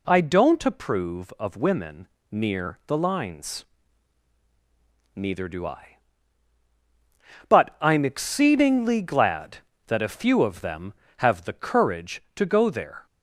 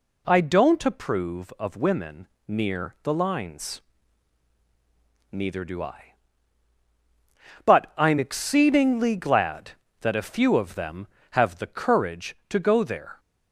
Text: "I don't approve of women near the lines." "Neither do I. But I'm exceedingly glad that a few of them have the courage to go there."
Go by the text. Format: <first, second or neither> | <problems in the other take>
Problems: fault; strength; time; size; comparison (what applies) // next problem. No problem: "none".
neither | pauses between "women" and "near"; slight; the same in both